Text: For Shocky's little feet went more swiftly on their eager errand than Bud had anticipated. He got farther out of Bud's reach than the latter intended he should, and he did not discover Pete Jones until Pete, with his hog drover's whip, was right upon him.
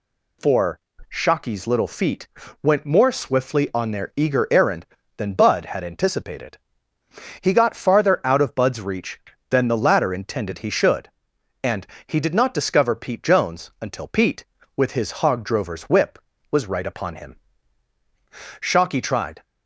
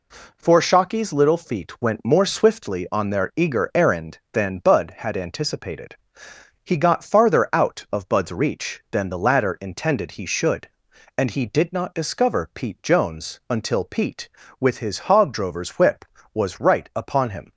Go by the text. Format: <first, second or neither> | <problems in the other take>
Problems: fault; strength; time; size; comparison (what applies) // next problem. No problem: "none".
second | pauses between "For" and "Shocky's"; slight; at 0.7 s; 0.30 s long // pauses between "feet" and "went"; slight; at 2.2 s; 0.34 s long // pauses between "and" and "he"; slight; at 11.8 s; 0.22 s long // goes on to say "Shocky tried"; noticeable; from 18.6 s on; 0.82 s long